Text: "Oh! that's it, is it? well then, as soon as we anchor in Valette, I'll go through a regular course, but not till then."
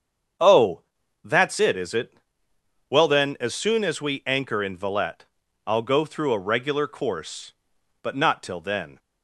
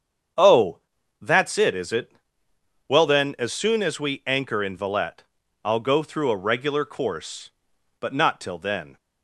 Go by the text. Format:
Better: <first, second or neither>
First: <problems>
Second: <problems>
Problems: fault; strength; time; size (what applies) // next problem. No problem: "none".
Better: neither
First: starts louder than the rest; strong; until 1.8 s; 7.5 dB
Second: starts louder than the rest; strong; until 1.7 s; 7.5 dB